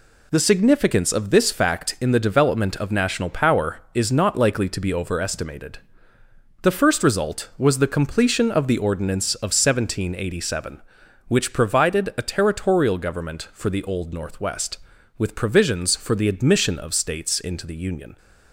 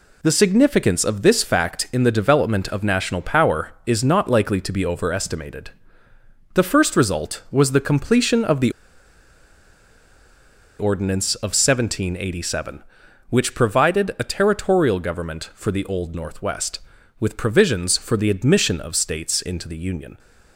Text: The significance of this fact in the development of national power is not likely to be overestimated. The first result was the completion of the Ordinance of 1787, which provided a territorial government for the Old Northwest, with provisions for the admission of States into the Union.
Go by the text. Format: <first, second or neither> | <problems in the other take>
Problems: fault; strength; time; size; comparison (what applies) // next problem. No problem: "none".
first | pauses between "the" and "Ordinance"; strong; at 8.6 s; 2.0 s long